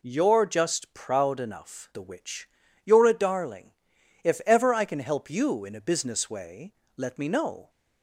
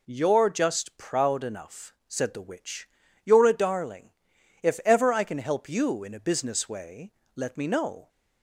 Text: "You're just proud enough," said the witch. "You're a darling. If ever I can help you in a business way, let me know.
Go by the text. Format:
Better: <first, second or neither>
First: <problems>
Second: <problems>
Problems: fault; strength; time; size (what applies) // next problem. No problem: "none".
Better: second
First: skips "said"; at 1.9 s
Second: none